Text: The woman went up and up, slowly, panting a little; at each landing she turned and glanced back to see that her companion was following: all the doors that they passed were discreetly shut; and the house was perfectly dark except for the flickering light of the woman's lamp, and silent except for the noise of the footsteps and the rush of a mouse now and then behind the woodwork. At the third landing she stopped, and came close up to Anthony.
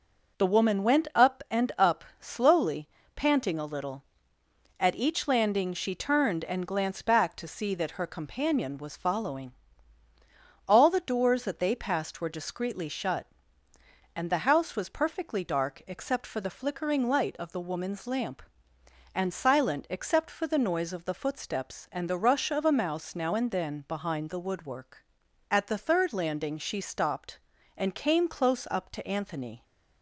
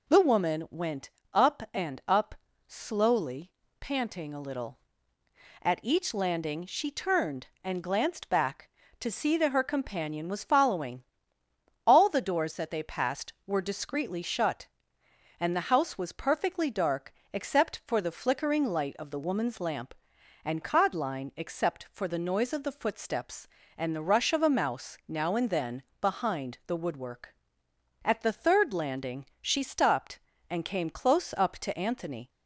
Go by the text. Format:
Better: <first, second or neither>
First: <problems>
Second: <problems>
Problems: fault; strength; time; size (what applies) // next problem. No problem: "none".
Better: first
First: none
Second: pauses between "went" and "up"; slight; at 1.0 s; 0.24 s long // pauses between "dark" and "except"; slight; at 17.1 s; 0.22 s long // says "codline" for "silent"; at 20.6 s // pauses between "then" and "behind"; slight; at 25.8 s; 0.18 s long // pauses between "landing" and "she"; slight; at 29.2 s; 0.16 s long